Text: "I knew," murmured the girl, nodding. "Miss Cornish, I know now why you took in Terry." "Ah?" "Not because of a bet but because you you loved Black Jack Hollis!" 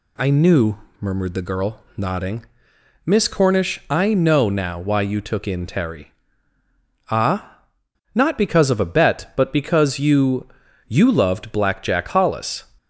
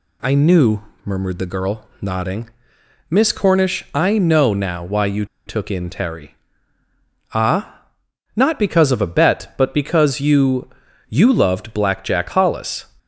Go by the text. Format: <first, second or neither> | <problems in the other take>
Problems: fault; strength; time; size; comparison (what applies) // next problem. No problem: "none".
first | pauses between "you" and "took"; slight; at 5.2 s; 0.21 s long // pauses between "you" and "you"; at 10.6 s; 0.42 s long; also in the first